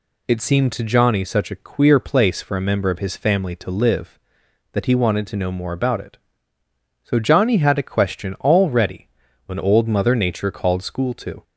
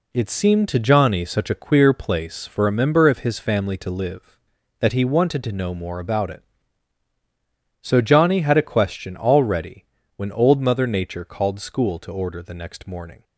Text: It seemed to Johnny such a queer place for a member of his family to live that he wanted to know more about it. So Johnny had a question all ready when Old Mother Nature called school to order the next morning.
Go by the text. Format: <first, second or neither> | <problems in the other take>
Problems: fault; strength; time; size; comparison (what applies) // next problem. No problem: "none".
second | pauses between "ready" and "when"; at 9.0 s; 0.38 s long; slight in the second // stops before "order the next morning"; at 11.4 s